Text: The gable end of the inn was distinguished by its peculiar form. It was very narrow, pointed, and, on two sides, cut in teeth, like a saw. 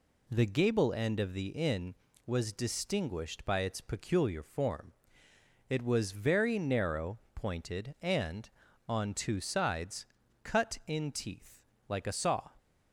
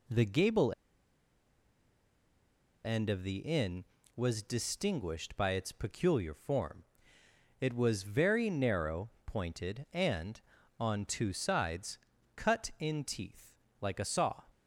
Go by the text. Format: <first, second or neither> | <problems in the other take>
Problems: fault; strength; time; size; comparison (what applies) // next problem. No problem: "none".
first | pauses between "gable" and "end"; strong; at 0.7 s; 2.1 s long